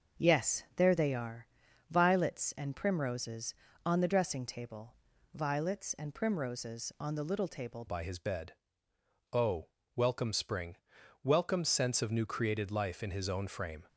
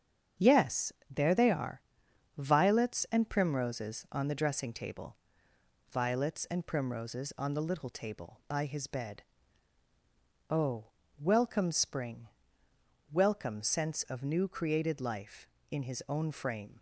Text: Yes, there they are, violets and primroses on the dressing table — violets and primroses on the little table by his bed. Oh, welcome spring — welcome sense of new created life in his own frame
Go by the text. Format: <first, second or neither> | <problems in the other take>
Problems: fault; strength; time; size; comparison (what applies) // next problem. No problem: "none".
second | starts louder than the rest; until 1.3 s; 6.5 dB; strong in the second // changes voice at "by"; from 7.8 s on; 6.0 s long